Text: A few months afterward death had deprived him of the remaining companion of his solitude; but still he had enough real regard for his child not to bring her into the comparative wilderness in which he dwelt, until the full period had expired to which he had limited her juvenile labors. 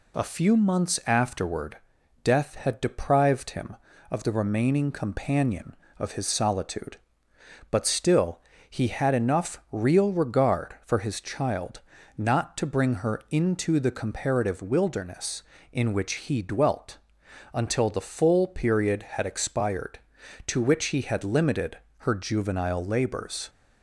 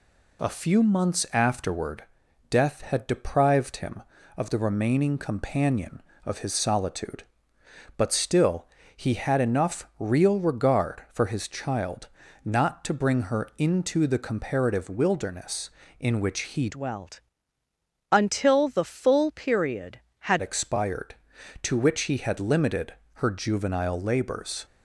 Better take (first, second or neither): first